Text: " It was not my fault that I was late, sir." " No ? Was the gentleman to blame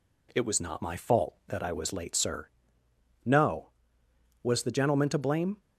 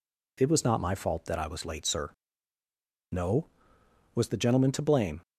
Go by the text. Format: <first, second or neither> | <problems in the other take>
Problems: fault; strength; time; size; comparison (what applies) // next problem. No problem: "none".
neither | none